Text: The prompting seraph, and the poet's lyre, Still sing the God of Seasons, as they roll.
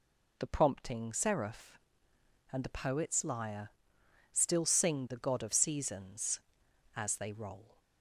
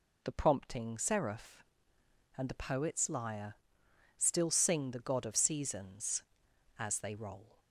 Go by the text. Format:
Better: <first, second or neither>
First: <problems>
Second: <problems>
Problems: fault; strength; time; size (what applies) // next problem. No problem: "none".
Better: neither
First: none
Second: none